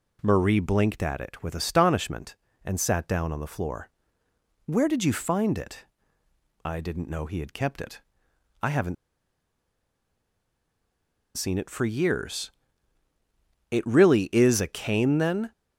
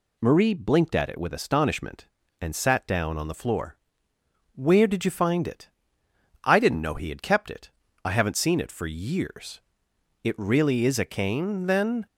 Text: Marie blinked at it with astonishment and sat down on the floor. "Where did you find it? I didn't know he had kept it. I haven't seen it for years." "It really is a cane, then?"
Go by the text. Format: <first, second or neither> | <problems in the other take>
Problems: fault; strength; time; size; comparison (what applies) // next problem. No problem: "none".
second | pauses between "haven't" and "seen"; strong; at 8.9 s; 2.4 s long